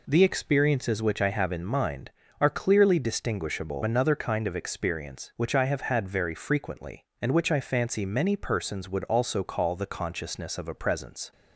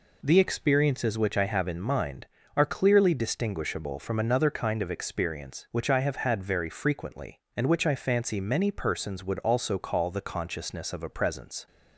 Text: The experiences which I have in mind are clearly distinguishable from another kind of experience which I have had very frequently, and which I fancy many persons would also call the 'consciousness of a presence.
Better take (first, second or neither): second